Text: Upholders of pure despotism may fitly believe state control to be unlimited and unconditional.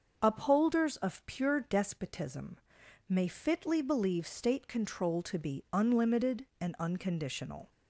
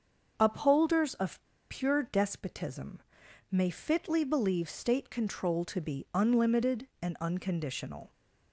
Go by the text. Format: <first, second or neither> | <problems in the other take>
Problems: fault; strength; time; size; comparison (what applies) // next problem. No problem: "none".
first | starts louder than the rest; until 1.3 s; 6.5 dB; also in the first // pauses between "of" and "pure"; slight; at 1.4 s; 0.29 s long // pauses between "despotism" and "may"; noticeable; at 2.9 s; 0.50 s long; noticeable in the first